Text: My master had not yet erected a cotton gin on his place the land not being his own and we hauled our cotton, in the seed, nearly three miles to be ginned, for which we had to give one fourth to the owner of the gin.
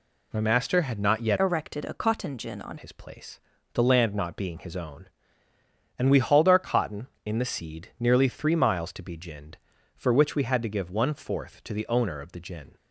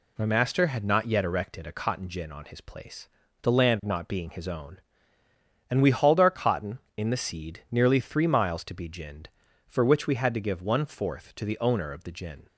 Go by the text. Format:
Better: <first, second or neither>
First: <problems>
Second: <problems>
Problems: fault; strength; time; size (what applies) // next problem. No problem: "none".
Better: second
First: changes voice from "erected" to "on"; from 1.3 to 2.7 s; 1.4 s long // pauses between "place" and "the"; slight; at 3.3 s; 0.34 s long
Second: pauses between "place" and "the"; slight; at 3.0 s; 0.34 s long